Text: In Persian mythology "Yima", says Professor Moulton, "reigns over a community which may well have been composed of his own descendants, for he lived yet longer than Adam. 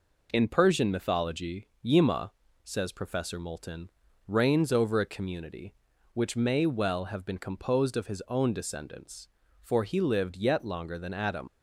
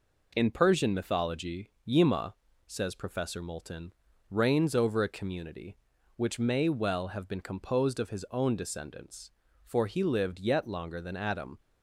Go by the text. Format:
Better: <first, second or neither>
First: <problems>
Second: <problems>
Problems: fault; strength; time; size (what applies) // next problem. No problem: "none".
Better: second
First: pauses between "mythology" and "Yima"; slight; at 1.6 s; 0.16 s long // leaves "Adam" unfinished; at 11.4 s; 90 ms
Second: pauses between "mythology" and "Yima"; slight; at 1.6 s; 0.16 s long